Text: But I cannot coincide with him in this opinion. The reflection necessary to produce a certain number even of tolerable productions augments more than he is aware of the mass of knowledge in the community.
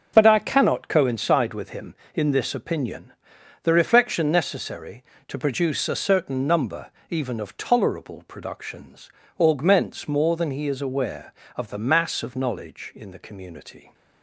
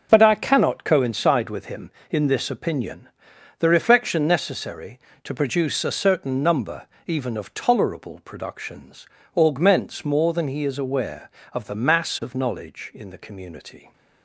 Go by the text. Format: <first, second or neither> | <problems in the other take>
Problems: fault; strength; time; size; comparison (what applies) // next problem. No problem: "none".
neither | starts louder than the rest; the same in both // pauses between "number" and "even"; slight; the same in both // pauses between "productions" and "augments"; slight; the same in both